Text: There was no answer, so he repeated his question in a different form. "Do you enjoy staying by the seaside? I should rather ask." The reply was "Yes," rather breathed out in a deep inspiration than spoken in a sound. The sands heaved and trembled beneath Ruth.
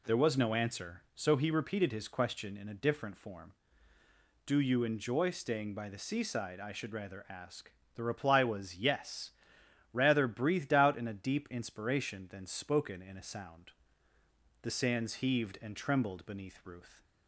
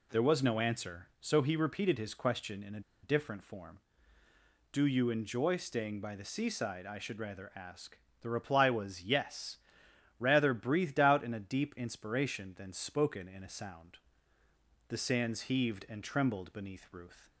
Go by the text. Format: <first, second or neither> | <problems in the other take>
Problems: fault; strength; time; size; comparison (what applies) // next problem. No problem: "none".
first | pauses between "a" and "different"; slight; at 2.8 s; 0.22 s long